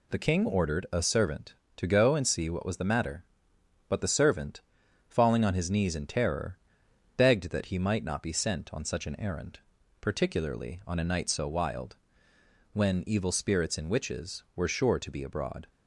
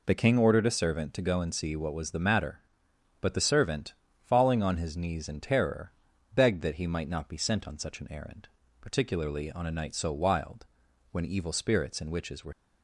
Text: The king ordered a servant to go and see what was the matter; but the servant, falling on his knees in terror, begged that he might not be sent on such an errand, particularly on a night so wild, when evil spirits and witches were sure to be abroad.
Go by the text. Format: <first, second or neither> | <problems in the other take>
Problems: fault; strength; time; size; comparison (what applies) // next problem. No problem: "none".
first | stops before "sure to be abroad"; at 12.5 s